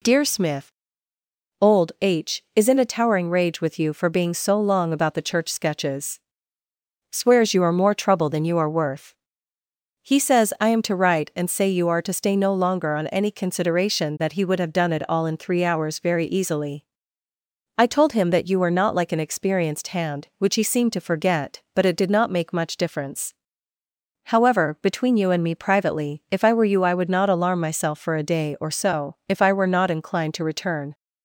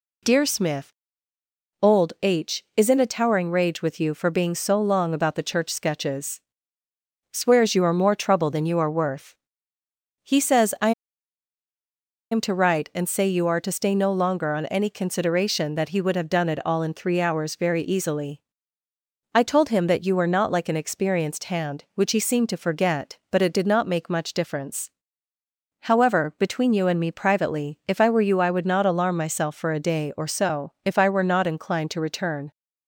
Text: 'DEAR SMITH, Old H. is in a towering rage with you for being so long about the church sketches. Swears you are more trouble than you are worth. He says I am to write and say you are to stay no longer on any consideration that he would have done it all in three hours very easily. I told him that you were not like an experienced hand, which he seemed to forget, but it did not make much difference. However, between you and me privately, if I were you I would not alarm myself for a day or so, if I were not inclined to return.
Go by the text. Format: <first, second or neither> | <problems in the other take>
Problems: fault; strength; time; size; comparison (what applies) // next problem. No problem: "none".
first | pauses between "I" and "am"; strong; at 10.9 s; 1.4 s long